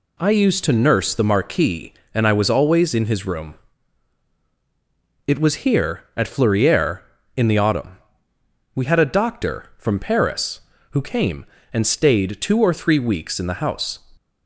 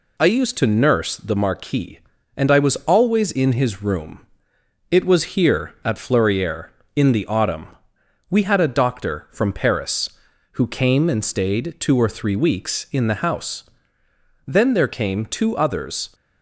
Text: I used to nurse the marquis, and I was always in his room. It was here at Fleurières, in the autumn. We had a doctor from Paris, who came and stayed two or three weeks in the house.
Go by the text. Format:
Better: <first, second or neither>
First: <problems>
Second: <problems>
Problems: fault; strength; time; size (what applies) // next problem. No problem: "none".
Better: first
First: none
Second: goes on to say "Then there came two others"; strong; from 14.4 s on; 1.6 s long